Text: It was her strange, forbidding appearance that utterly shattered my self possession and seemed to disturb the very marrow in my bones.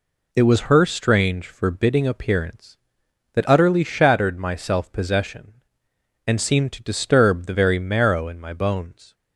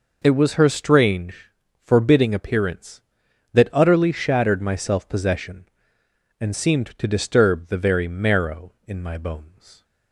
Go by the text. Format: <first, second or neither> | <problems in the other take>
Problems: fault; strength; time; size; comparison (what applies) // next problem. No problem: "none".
neither | none